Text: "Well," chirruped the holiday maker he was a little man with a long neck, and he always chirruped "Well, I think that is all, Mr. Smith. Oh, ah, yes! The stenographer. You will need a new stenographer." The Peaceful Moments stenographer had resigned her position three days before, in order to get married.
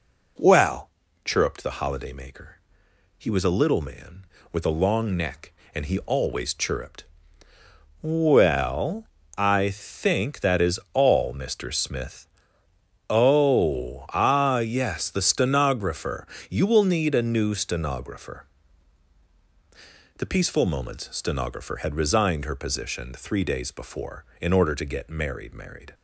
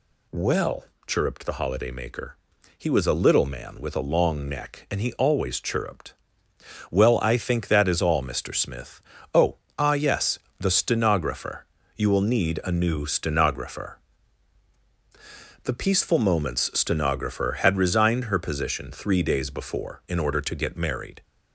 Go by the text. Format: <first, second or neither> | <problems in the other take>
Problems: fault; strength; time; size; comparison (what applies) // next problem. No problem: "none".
second | pauses between "maker" and "he"; noticeable; at 2.5 s; 0.60 s long; noticeable in the second // pauses between "chirruped" and "Well"; noticeable; at 7.0 s; 0.96 s long; noticeable in the second // says "married" twice; at 25.5 s